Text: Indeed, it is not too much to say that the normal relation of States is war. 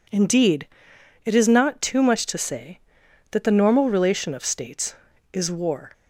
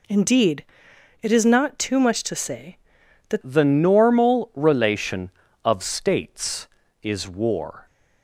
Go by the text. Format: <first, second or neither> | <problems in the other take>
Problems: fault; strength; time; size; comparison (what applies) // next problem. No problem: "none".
first | changes voice at "the"; from 3.4 s on; 4.4 s long